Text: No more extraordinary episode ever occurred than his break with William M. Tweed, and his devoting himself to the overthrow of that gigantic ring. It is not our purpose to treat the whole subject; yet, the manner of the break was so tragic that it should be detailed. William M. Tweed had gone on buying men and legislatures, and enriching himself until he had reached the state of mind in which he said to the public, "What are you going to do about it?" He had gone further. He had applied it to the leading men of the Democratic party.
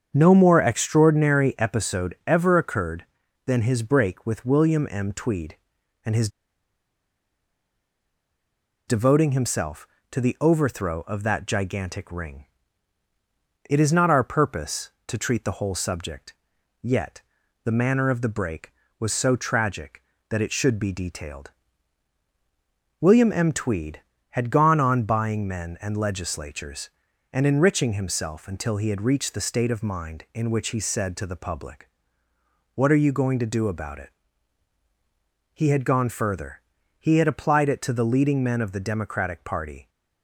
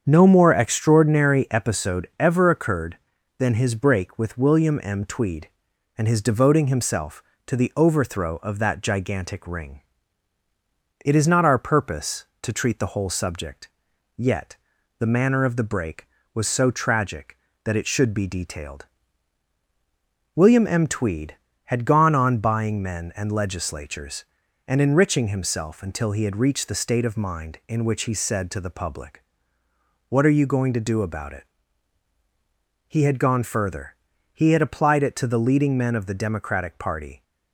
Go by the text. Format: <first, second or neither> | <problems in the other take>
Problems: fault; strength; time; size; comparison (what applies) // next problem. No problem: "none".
second | starts louder than the rest; strong; until 1.1 s; 7.5 dB; strong in the second // pauses between "his" and "devoting"; strong; at 6.2 s; 2.5 s long